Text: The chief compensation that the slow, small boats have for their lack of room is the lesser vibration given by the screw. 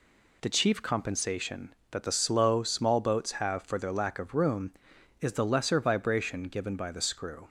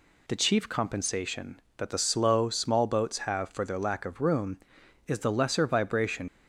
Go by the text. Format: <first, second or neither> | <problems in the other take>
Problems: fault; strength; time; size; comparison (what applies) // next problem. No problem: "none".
first | stops before "given by the screw"; at 6.2 s